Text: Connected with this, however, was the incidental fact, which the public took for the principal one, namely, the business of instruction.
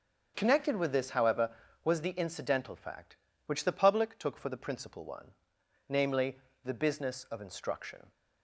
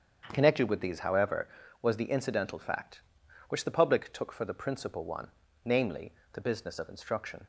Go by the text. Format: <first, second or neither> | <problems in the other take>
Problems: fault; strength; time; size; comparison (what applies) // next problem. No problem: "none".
first | starts louder than the rest; strong; until 1.3 s; 7.5 dB; strong in the first // says "these" for "this"; at 0.7 s